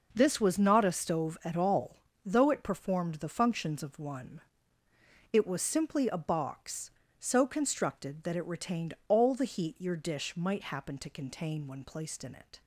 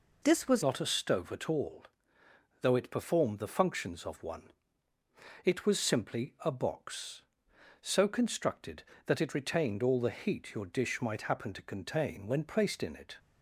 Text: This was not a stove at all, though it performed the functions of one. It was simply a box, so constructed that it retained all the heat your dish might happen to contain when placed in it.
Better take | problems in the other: first | changes voice at "not"; from 0.6 s on; 12.5 s long

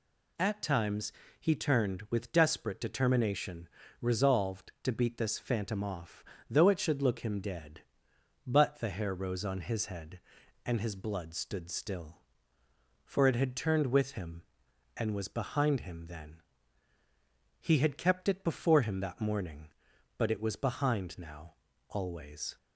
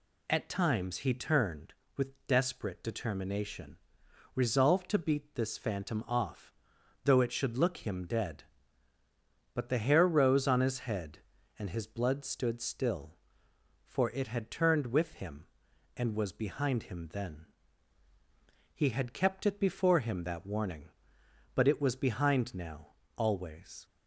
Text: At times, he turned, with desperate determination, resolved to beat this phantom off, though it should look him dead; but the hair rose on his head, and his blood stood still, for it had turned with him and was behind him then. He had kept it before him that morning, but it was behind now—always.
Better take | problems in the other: first | says "warning" for "morning"; at 20.4 s

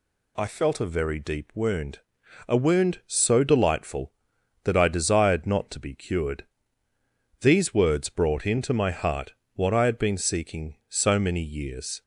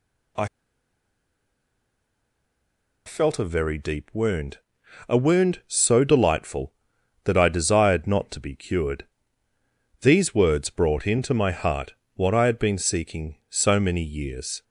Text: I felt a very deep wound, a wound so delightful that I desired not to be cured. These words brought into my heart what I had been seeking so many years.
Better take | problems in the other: first | pauses between "I" and "felt"; strong; at 0.4 s; 2.5 s long // pauses between "heart" and "what"; slight; at 11.9 s; 0.20 s long; slight in the first

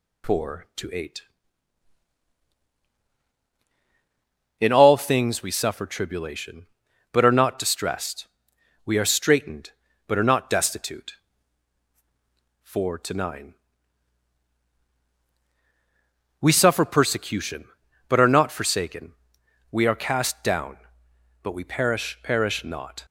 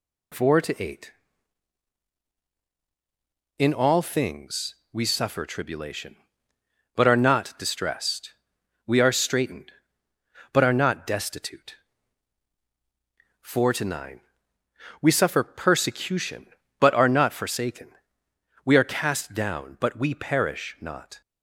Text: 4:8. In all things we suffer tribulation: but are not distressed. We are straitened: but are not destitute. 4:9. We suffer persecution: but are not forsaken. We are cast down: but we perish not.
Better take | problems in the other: second | says "perish" twice; at 22.2 s

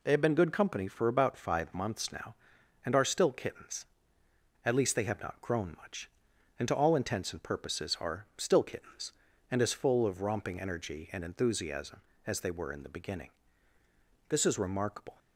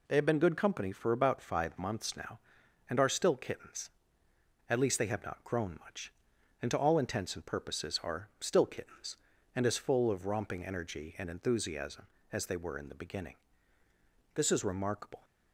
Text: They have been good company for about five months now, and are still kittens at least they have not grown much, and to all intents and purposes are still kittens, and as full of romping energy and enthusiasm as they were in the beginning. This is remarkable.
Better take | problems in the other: neither | none

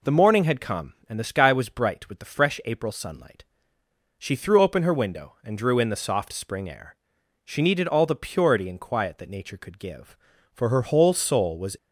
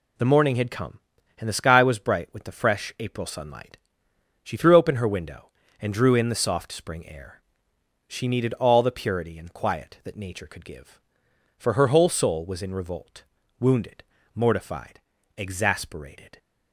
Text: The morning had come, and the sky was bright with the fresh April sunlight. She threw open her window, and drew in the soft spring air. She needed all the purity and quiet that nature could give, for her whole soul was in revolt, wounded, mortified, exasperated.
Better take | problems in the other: second | stops before "in revolt wounded mortified exasperated"; at 11.7 s

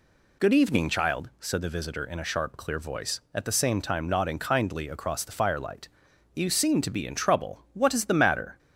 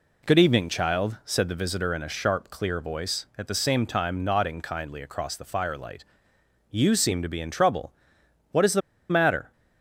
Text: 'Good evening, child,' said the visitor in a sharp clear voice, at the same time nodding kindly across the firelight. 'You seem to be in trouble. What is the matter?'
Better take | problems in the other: first | pauses between "the" and "matter"; slight; at 8.8 s; 0.29 s long

